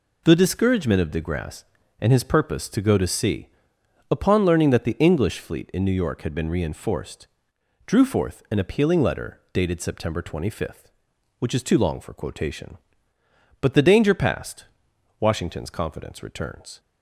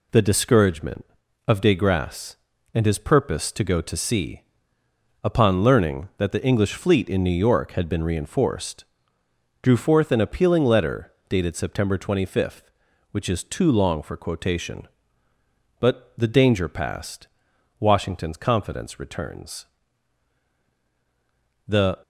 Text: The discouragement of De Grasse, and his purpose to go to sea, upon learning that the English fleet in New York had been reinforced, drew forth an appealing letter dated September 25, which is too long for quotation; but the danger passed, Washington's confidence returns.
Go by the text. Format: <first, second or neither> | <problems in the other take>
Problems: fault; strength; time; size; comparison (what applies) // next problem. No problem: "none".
first | pauses between "letter" and "dated"; slight; at 11.1 s; 0.16 s long // goes on to say "The"; slight; from 21.6 s on; 0.32 s long